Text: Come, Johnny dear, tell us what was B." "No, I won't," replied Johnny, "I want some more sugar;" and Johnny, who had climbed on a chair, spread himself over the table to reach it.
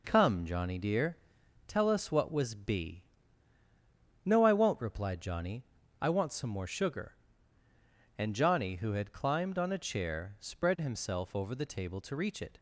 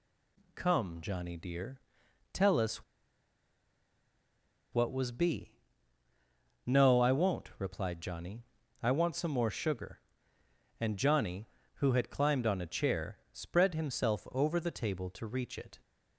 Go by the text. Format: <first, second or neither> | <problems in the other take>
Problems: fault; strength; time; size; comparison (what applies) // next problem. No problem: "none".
first | pauses between "us" and "what"; strong; at 2.8 s; 1.8 s long